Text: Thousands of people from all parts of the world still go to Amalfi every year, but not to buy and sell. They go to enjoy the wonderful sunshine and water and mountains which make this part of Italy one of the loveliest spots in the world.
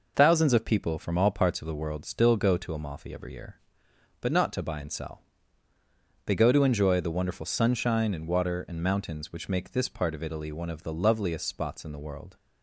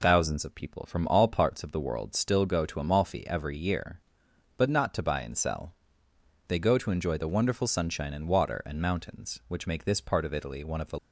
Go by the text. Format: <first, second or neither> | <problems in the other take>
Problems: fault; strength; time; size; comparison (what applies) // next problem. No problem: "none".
first | stops before "loveliest spots in the world"; at 10.9 s